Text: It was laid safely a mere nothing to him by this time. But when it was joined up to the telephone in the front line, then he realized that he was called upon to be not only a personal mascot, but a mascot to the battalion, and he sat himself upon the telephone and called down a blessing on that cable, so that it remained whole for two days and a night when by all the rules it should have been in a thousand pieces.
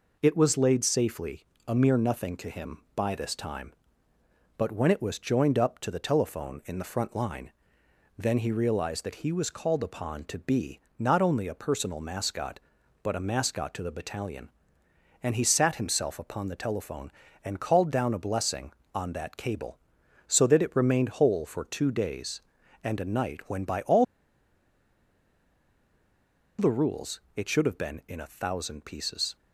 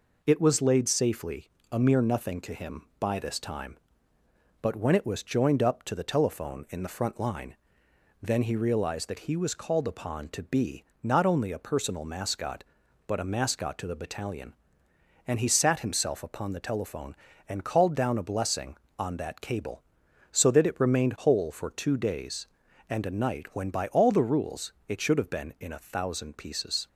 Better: second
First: pauses between "safely" and "a"; slight; at 1.4 s; 0.22 s long // pauses between "be" and "not"; slight; at 10.7 s; 0.18 s long // pauses between "all" and "the"; strong; at 24.0 s; 2.5 s long // pauses between "rules" and "it"; slight; at 27.1 s; 0.16 s long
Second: pauses between "safely" and "a"; slight; at 1.5 s; 0.22 s long // pauses between "be" and "not"; slight; at 10.8 s; 0.18 s long // pauses between "rules" and "it"; slight; at 24.7 s; 0.16 s long

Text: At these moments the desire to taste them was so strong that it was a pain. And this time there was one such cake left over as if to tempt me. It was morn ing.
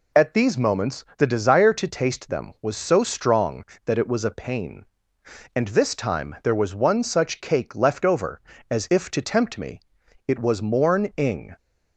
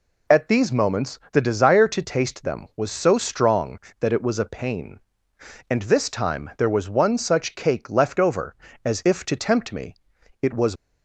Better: first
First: none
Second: stops before "morn ing"; at 10.7 s

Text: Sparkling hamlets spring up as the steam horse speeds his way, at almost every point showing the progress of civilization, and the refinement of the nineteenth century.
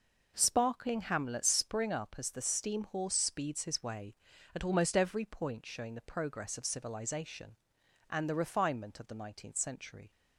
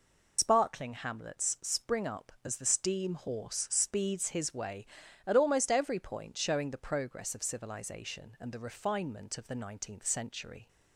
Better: first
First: none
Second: loses the start of "Sparkling"; at 0.3 s; 90 ms

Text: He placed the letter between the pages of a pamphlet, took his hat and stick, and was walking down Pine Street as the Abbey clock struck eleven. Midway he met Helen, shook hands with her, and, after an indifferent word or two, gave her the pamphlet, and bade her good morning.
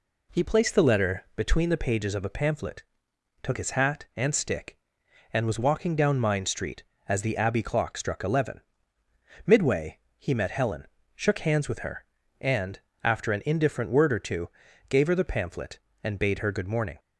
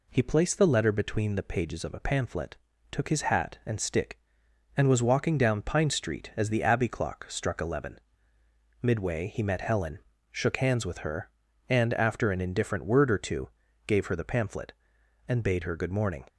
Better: second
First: says "Mine" for "Pine"; at 6.1 s // pauses between "Midway" and "he"; slight; at 9.9 s; 0.20 s long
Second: none

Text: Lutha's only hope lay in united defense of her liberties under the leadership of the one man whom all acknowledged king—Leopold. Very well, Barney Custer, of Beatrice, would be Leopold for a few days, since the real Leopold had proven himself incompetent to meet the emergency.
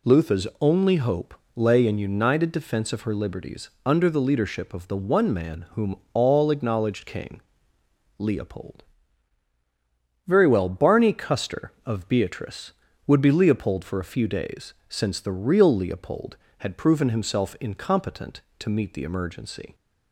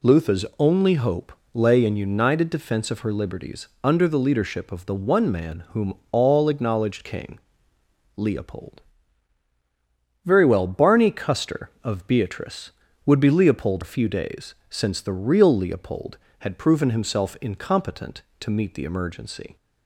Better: first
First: pauses between "hope" and "lay"; slight; at 1.3 s; 0.24 s long // pauses between "liberties" and "under"; slight; at 3.6 s; 0.16 s long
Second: pauses between "hope" and "lay"; slight; at 1.3 s; 0.24 s long // pauses between "liberties" and "under"; slight; at 3.6 s; 0.16 s long // skips "for"; at 13.8 s

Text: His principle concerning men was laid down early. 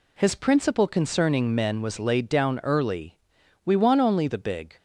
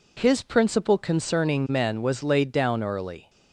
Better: second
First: goes on to say "We want only the big"; noticeable; from 3.6 s on; 1.1 s long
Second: none

